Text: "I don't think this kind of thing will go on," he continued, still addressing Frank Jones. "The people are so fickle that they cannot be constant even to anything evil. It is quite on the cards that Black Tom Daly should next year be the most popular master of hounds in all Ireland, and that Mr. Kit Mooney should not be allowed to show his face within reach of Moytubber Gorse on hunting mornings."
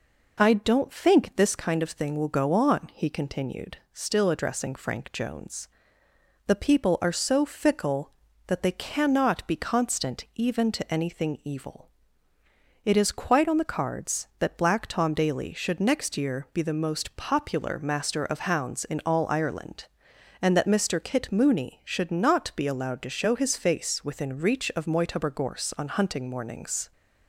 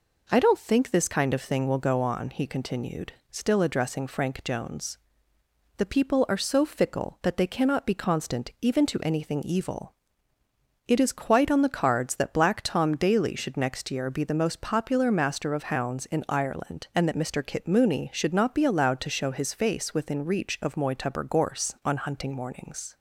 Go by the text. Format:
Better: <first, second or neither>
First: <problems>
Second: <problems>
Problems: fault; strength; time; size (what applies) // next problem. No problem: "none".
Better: first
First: none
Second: skips "all"; at 16.2 s